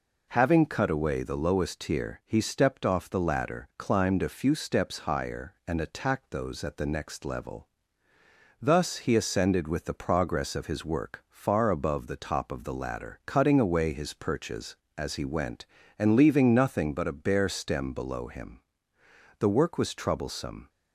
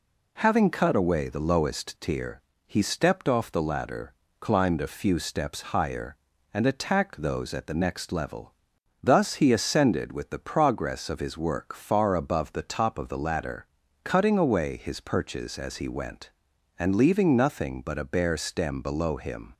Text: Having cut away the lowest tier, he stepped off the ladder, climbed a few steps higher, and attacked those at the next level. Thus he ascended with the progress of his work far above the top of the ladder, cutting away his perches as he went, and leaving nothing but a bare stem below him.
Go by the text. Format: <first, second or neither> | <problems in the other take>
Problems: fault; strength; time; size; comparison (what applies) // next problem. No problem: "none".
second | goes on to say "The work was troublesome"; noticeable; from 19.3 s on; 1.3 s long